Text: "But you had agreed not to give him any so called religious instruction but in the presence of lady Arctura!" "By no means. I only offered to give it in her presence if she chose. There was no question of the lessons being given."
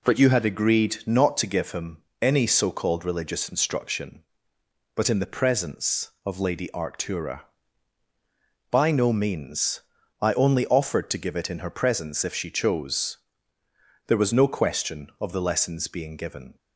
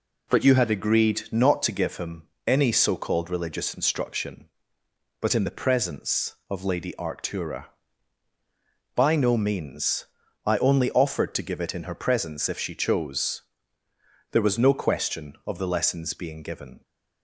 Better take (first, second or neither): neither